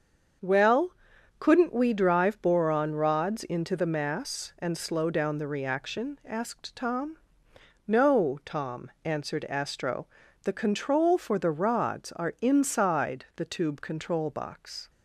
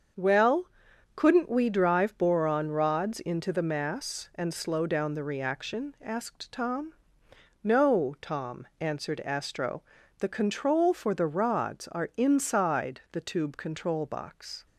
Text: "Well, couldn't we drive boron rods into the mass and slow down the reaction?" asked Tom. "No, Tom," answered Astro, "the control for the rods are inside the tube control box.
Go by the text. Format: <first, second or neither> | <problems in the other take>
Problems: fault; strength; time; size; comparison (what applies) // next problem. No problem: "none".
neither | starts louder than the rest; the same in both